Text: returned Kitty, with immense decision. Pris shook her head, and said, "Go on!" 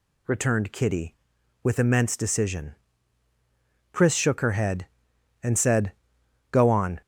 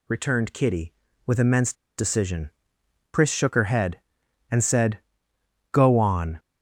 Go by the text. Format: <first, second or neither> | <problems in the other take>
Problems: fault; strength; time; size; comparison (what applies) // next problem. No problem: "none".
first | pauses between "immense" and "decision"; slight; at 1.7 s; 0.24 s long